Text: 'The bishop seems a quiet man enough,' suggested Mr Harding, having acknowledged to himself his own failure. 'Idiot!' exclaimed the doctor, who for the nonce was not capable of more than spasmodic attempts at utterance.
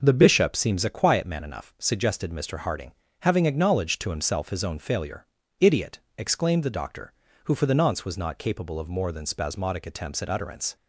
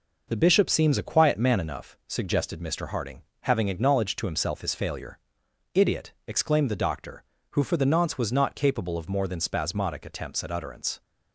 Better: first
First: none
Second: skips "own"; at 4.7 s

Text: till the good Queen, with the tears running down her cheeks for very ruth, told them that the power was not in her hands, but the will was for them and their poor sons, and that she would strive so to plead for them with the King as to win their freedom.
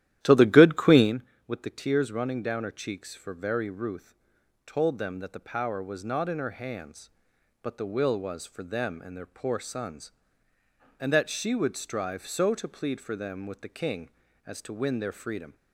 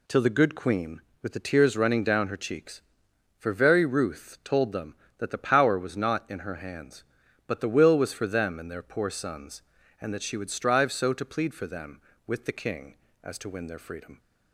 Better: second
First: starts louder than the rest; strong; until 1.1 s; 12.5 dB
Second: none

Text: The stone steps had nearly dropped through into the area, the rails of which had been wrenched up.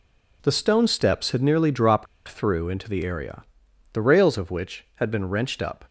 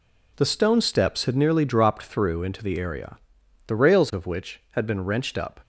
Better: second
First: pauses between "dropped" and "through"; slight; at 2.0 s; 0.21 s long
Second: none

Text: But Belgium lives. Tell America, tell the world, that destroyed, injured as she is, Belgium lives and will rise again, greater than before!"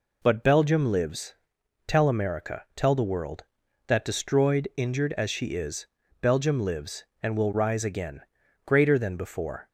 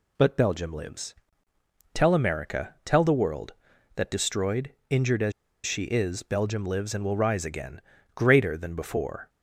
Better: first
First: none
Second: pauses between "as" and "she"; slight; at 5.3 s; 0.34 s long

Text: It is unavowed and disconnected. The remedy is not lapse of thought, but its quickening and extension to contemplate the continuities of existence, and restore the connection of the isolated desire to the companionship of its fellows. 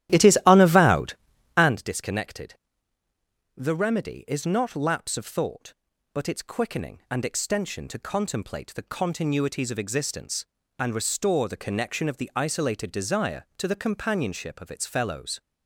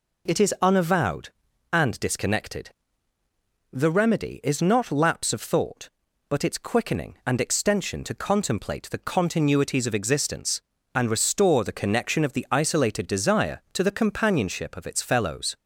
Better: second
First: starts louder than the rest; strong; until 1.8 s; 13.5 dB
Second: none

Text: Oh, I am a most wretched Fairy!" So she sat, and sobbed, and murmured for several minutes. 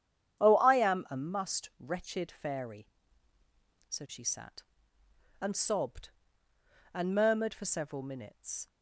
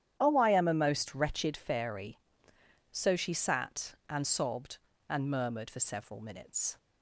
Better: second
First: starts louder than the rest; strong; until 1.4 s; 9 dB // says "must" for "most"; at 1.1 s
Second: starts louder than the rest; strong; until 1.2 s; 10 dB

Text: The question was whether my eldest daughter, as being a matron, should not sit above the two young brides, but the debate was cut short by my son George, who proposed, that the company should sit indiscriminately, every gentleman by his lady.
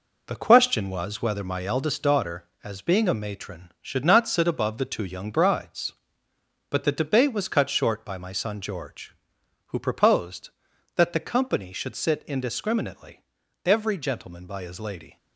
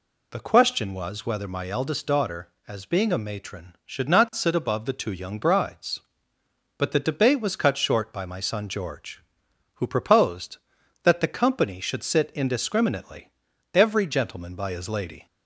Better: second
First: gets quieter; throughout; 6.5 dB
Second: none

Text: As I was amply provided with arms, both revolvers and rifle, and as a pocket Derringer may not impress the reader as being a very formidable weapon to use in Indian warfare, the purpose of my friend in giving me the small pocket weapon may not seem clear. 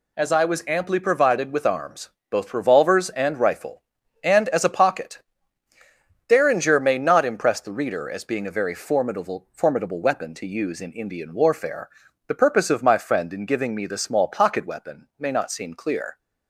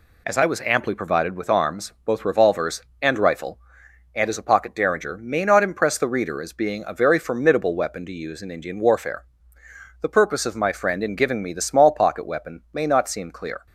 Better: second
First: pauses between "pocket" and "Derringer"; at 5.2 s; 1.0 s long // says "formidable" twice; at 9.5 s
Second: none

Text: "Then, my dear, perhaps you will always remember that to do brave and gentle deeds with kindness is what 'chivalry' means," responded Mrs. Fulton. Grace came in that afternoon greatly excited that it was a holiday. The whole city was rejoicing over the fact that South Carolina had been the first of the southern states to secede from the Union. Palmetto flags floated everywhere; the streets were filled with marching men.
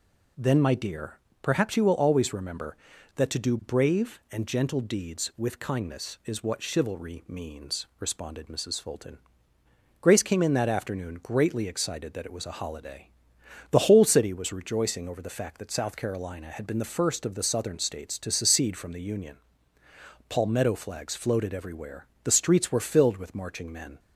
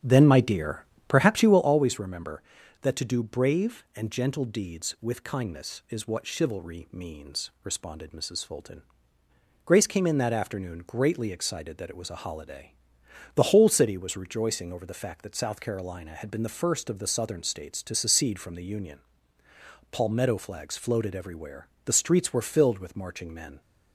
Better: first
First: none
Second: starts louder than the rest; strong; until 1.8 s; 9 dB

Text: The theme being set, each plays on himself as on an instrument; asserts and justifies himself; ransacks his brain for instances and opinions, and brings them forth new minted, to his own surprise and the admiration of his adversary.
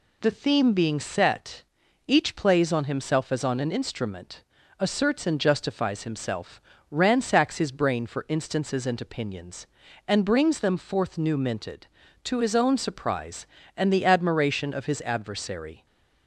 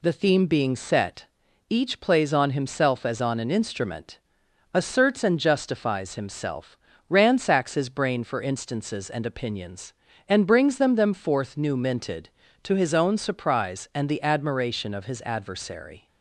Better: first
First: none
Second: says "them" twice; at 10.9 s

